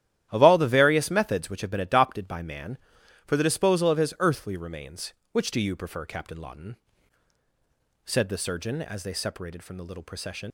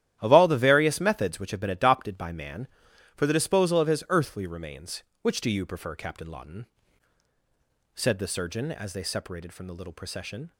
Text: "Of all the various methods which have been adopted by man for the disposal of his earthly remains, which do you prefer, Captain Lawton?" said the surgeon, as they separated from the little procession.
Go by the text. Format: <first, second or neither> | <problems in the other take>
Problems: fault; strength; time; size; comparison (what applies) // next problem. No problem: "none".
second | starts louder than the rest; strong; until 1.3 s; 12 dB; strong in the second // leaves "procession" unfinished; at 10.4 s; 120 ms